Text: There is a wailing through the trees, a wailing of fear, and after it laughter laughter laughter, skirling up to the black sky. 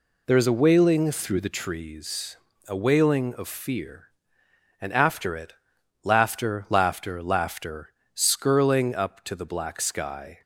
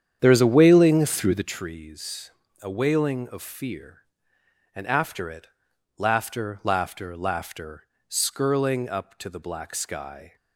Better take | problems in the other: first | starts louder than the rest; strong; until 1.6 s; 8.5 dB // pauses between "it" and "laughter"; noticeable; at 5.4 s; 0.50 s long; noticeable in the first

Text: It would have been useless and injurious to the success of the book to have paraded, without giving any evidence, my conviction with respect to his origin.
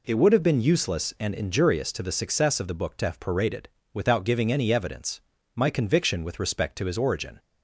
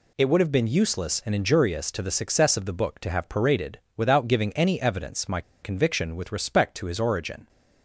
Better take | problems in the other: first | pauses between "my" and "conviction"; slight; at 5.4 s; 0.21 s long

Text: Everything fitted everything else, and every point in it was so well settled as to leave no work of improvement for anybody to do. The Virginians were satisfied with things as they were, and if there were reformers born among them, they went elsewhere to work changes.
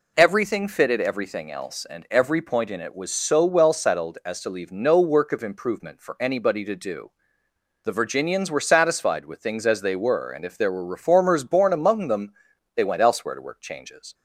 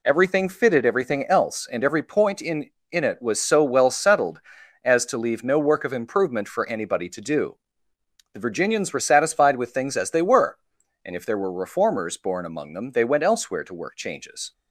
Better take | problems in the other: first | says "in" twice; at 2.9 s

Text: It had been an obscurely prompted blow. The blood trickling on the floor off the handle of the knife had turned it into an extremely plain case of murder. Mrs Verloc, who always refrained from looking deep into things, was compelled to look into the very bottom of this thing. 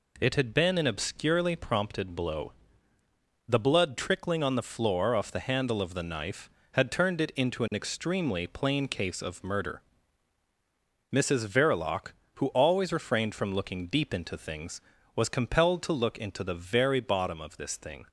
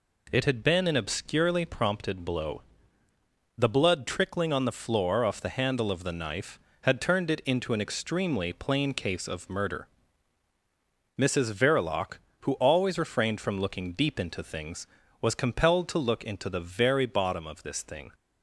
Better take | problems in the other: neither | none

